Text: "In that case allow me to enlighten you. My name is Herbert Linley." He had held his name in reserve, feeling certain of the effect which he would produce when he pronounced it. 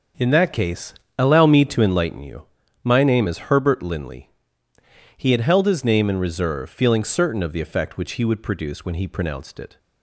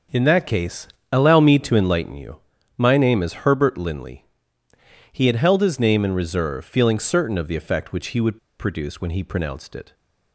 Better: first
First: starts louder than the rest; until 1.4 s; 6.5 dB // pauses between "case" and "allow"; slight; at 0.9 s; 0.24 s long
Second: starts louder than the rest; until 1.3 s; 6.5 dB // pauses between "case" and "allow"; slight; at 0.8 s; 0.24 s long // pauses between "would" and "produce"; slight; at 8.3 s; 0.20 s long

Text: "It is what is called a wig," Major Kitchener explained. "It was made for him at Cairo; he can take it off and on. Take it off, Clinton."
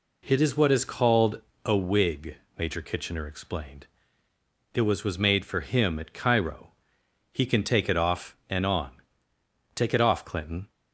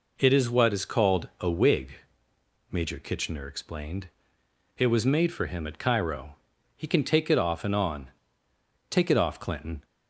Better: second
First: pauses between "called" and "a"; slight; at 1.4 s; 0.24 s long // says "was" twice; at 5.0 s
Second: none

